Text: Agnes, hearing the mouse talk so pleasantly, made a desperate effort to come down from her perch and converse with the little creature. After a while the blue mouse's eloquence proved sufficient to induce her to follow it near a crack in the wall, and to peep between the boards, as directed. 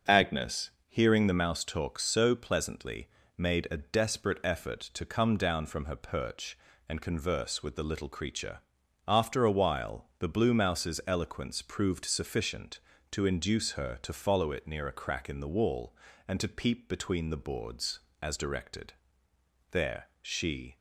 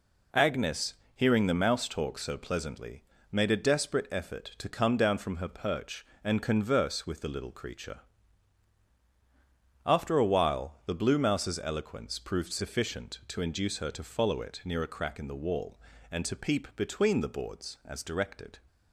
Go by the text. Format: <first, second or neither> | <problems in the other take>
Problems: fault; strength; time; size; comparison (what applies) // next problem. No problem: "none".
second | starts louder than the rest; until 1.2 s; 6.5 dB // pauses between "while" and "the"; slight; at 10.0 s; 0.16 s long // goes on to say "There she"; noticeable; from 19.7 s on; 1.0 s long